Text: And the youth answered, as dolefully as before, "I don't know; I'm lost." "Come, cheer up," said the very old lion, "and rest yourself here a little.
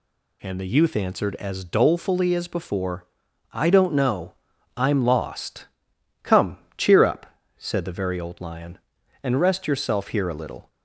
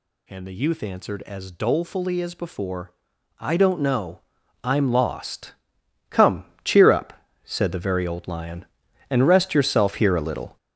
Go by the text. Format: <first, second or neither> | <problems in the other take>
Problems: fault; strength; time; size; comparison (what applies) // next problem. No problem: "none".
first | gets louder; strong; throughout; 7.5 dB